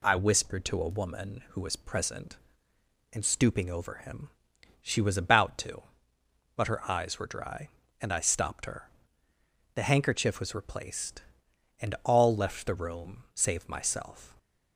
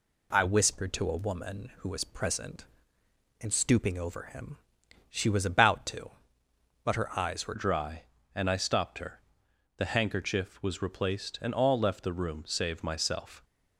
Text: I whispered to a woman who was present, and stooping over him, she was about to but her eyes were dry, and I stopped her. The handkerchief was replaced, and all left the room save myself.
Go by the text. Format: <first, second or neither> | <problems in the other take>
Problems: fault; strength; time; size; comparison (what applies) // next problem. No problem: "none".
first | changes voice at "dry"; from 7.5 s on; 5.9 s long